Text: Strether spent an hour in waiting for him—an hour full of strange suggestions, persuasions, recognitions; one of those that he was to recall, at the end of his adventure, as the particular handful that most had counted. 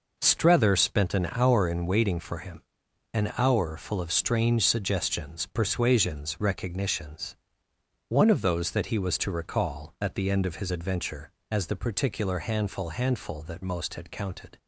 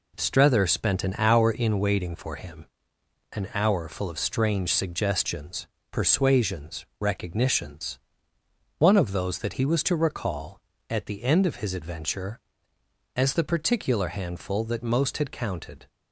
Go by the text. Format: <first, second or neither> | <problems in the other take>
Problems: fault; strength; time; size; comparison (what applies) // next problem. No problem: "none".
second | says "handful" twice; at 12.8 s